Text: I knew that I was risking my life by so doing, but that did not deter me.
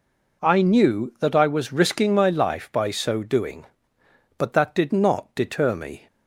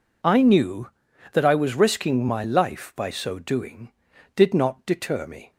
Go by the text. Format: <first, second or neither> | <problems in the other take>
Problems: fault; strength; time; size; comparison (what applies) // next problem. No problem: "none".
first | skips "but that"; at 4.1 s